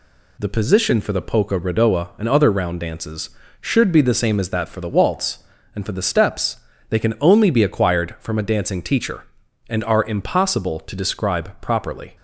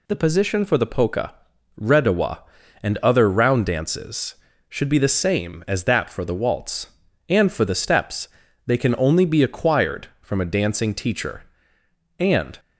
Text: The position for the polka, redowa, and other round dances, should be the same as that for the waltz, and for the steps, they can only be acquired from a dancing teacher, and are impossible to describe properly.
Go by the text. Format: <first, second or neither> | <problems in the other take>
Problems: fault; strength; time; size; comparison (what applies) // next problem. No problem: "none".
first | stops before "are impossible to describe properly"; at 12.5 s